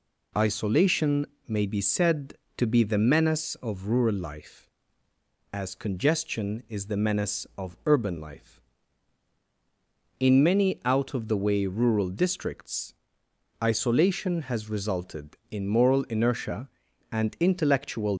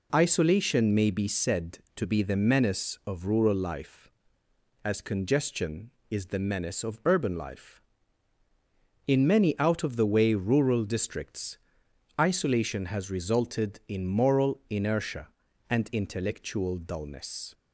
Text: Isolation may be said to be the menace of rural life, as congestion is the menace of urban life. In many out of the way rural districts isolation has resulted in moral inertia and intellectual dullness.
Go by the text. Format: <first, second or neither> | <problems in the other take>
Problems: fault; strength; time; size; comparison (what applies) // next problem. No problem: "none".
second | pauses between "Isolation" and "may"; slight; at 1.2 s; 0.22 s long // pauses between "districts" and "isolation"; noticeable; at 12.9 s; 0.68 s long; noticeable in the second // stops before "dullness"; at 18.1 s